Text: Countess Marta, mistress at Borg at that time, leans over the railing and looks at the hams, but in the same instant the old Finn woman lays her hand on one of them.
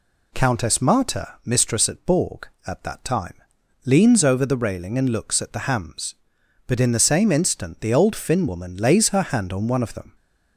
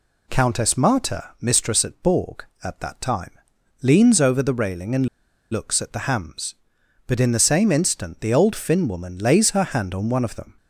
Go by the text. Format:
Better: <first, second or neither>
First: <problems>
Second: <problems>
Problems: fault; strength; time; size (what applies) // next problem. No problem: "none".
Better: first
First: none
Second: pauses between "and" and "looks"; at 5.0 s; 0.44 s long